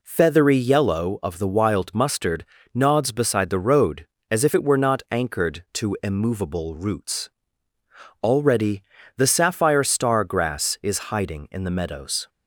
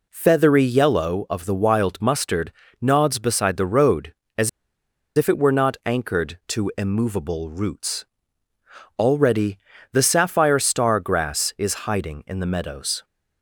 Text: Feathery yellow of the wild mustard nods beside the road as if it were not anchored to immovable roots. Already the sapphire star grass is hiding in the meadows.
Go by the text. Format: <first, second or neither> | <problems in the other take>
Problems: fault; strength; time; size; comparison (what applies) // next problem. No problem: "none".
first | pauses between "mustard" and "nods"; slight; at 2.5 s; 0.30 s long; slight in the first // pauses between "as" and "if"; noticeable; at 4.4 s; 0.67 s long // pauses between "Already" and "the"; slight; at 9.5 s; 0.36 s long; slight in the first